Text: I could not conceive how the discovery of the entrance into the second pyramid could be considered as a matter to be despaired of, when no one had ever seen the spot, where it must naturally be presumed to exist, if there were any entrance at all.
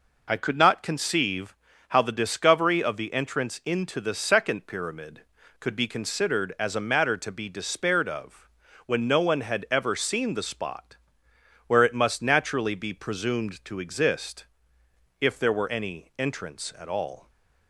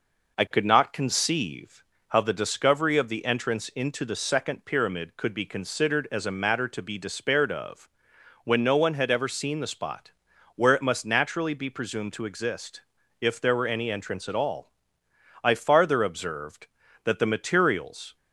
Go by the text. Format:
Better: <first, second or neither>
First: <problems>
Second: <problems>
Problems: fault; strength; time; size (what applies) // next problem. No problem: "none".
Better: first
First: pauses between "conceive" and "how"; slight; at 1.5 s; 0.34 s long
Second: pauses between "conceive" and "how"; slight; at 1.8 s; 0.28 s long // goes on to say "I farther observed that the materials"; strong; from 15.4 s on; 2.7 s long